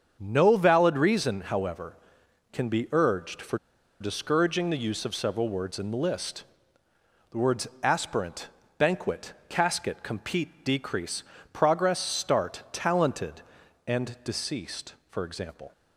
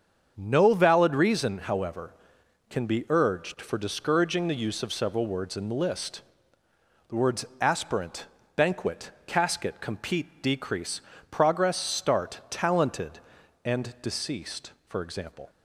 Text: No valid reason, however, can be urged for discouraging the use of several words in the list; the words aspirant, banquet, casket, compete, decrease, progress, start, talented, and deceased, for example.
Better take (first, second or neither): second